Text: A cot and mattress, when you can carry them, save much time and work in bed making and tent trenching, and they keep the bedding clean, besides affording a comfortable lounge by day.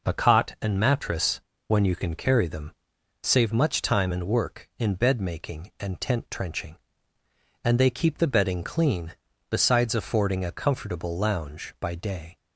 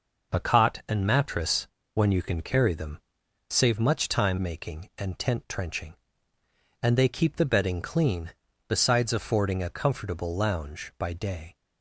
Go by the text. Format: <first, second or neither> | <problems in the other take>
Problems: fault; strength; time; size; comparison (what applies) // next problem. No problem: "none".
first | skips "and work in bed"; at 4.3 s